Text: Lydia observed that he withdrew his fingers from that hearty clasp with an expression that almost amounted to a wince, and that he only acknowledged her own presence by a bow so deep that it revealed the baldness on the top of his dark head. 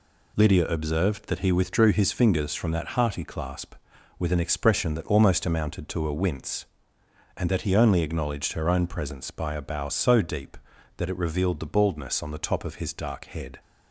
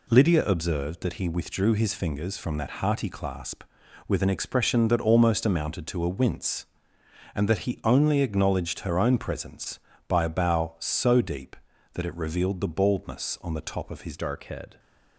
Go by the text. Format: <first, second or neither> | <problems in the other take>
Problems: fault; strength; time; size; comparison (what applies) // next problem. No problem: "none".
first | changes voice at "dark"; from 14.1 s on; 0.6 s long